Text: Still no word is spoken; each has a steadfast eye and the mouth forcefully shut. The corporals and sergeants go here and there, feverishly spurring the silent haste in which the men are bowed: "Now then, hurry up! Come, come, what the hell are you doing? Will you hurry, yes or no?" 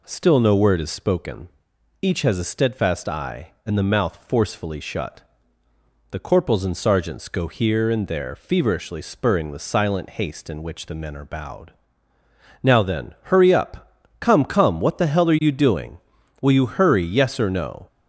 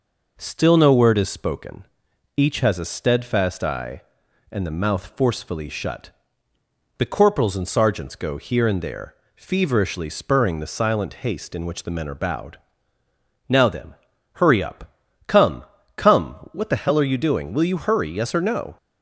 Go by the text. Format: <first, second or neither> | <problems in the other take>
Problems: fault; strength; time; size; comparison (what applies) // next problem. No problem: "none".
neither | none